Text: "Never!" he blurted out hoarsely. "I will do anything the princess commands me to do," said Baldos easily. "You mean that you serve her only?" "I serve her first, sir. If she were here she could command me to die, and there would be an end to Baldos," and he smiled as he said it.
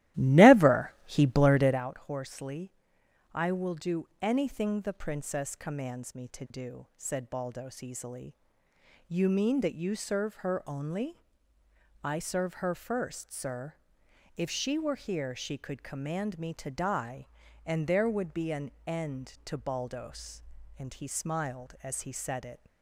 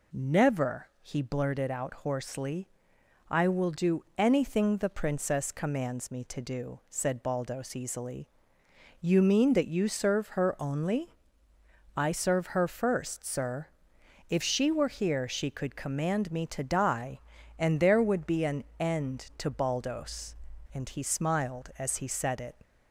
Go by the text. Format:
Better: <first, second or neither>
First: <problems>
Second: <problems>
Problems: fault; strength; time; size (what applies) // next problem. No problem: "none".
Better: second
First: starts louder than the rest; strong; until 1.9 s; 15 dB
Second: none